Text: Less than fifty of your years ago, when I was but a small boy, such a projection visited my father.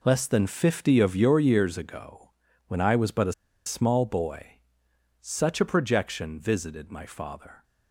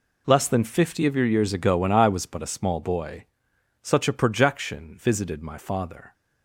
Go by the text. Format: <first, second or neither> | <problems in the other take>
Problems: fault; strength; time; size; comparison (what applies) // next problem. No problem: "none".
second | pauses between "a" and "small"; slight; at 3.3 s; 0.32 s long